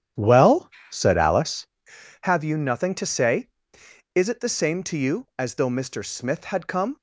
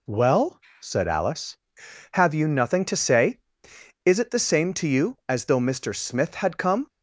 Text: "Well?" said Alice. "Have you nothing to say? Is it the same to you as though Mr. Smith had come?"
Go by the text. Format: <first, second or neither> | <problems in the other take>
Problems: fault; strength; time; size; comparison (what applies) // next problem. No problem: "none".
second | starts louder than the rest; strong; until 1.8 s; 10 dB